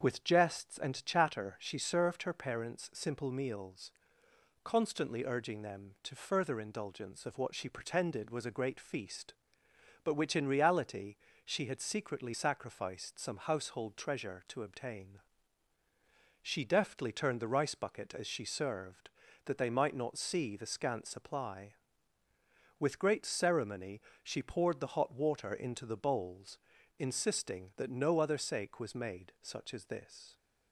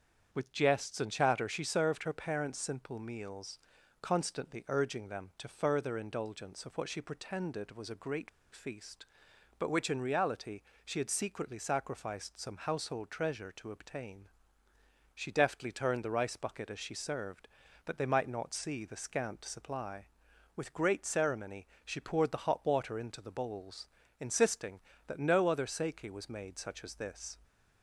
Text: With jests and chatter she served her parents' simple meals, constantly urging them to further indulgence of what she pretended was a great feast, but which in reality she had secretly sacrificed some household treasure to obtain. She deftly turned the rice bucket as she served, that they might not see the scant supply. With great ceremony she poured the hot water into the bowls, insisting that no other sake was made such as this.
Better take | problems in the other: first | starts louder than the rest; strong; until 1.3 s; 7.5 dB; also in the first // pauses between "great" and "feast"; slight; at 8.2 s; 0.24 s long // pauses between "reality" and "she"; slight; at 10.6 s; 0.22 s long; slight in the first // pauses between "ceremony" and "she"; slight; at 21.6 s; 0.18 s long; slight in the first

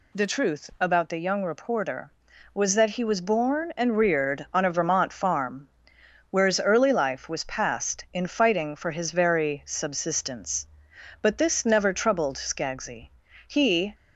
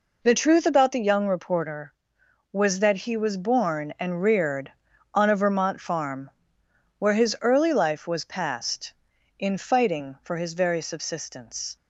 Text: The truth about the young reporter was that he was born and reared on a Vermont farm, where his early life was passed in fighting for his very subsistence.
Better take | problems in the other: second | goes on to say "But this never troubled Skaggsy He"; strong; from 11.2 s on; 2.7 s long

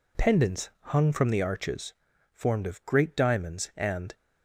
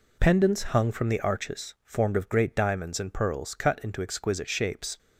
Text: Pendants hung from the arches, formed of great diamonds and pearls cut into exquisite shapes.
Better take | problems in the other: second | stops before "pearls cut into exquisite shapes"; at 4.1 s

